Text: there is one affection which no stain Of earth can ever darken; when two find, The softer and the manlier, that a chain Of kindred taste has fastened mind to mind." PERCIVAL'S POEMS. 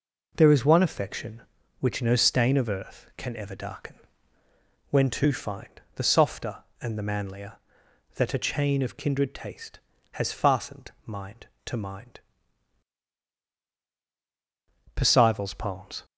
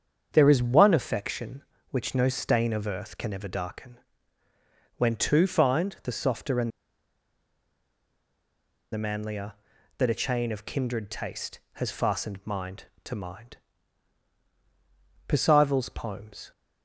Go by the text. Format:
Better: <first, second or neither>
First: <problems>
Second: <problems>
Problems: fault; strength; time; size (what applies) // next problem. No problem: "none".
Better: first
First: none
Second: starts louder than the rest; strong; until 1.3 s; 7.5 dB // pauses between "and" and "the"; strong; at 6.7 s; 2.2 s long